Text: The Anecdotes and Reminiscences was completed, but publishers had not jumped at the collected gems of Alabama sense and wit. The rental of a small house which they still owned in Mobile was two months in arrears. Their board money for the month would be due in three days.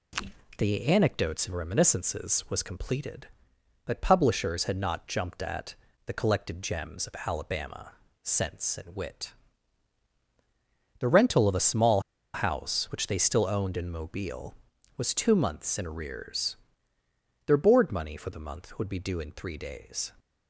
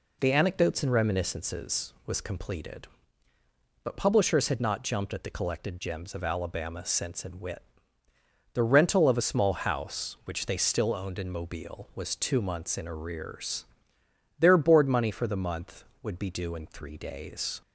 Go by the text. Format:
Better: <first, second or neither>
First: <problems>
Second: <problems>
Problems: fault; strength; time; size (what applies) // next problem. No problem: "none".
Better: second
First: pauses between "at" and "the"; slight; at 5.7 s; 0.32 s long // pauses between "Alabama" and "sense"; slight; at 7.9 s; 0.34 s long // pauses between "small" and "house"; slight; at 11.9 s; 0.34 s long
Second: none